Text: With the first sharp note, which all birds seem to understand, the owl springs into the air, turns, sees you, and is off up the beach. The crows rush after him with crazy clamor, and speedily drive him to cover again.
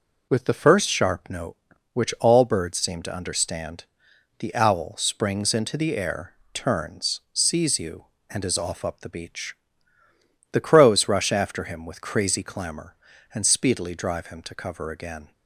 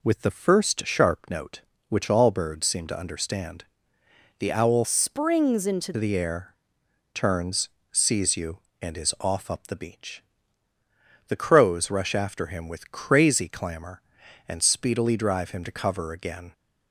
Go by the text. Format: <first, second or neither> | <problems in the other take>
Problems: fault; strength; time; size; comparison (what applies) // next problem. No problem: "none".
first | changes voice from "springs" to "into"; from 4.8 to 5.9 s; 1.1 s long